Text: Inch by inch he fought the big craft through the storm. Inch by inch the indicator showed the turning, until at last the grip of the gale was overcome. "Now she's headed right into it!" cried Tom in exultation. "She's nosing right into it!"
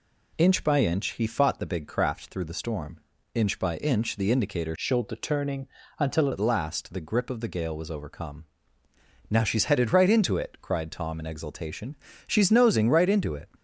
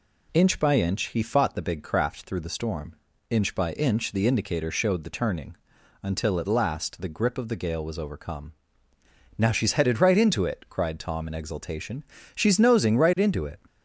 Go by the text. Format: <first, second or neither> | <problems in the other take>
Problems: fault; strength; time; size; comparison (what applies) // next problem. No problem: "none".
second | changes voice from "showed" to "until"; from 4.7 to 6.2 s; 1.5 s long